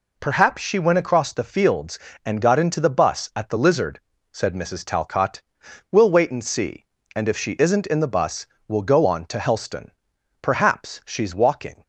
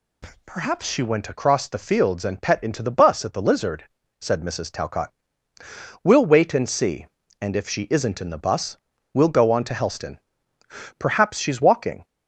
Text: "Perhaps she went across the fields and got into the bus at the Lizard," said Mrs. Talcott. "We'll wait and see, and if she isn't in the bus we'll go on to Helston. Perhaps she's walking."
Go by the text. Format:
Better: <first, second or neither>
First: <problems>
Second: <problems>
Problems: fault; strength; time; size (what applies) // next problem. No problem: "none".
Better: first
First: pauses between "bus" and "we'll"; slight; at 8.4 s; 0.20 s long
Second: says "pet" for "got"; at 2.4 s // pauses between "bus" and "we'll"; slight; at 8.7 s; 0.36 s long